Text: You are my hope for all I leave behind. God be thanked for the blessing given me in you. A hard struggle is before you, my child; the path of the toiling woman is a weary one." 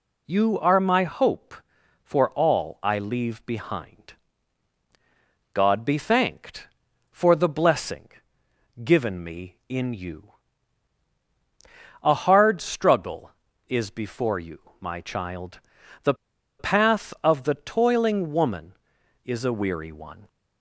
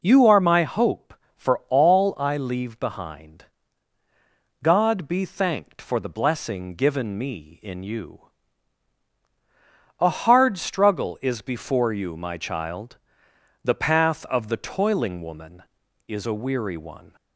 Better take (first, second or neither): second